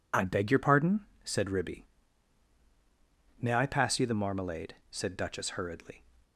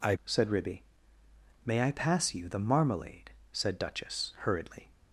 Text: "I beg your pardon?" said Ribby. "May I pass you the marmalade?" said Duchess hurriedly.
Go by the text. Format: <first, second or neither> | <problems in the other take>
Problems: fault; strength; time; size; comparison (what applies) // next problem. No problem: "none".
first | skips "beg your pardon"; at 0.2 s